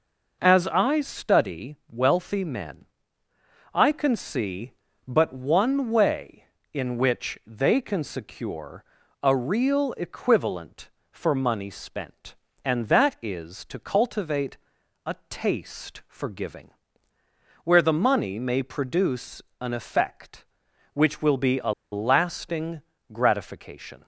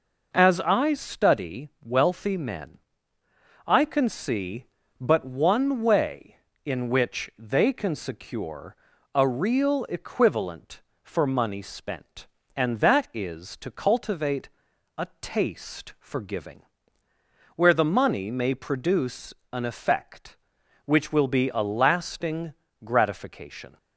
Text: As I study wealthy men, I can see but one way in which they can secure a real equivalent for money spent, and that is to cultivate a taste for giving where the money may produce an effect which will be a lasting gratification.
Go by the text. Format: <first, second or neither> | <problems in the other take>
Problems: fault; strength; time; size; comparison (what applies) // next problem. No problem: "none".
second | pauses between "secure" and "a"; at 8.8 s; 0.38 s long; also in the second // pauses between "cultivate" and "a"; noticeable; at 14.5 s; 0.48 s long; noticeable in the second // pauses between "a" and "taste"; slight; at 15.1 s; 0.16 s long; slight in the second // pauses between "giving" and "where"; noticeable; at 16.6 s; 0.96 s long; noticeable in the second // pauses between "produce" and "an"; slight; at 19.4 s; 0.18 s long; slight in the second // pauses between "a" and "lasting"; slight; at 21.7 s; 0.19 s long // pauses between "lasting" and "gratification"; slight; at 22.8 s; 0.30 s long; slight in the second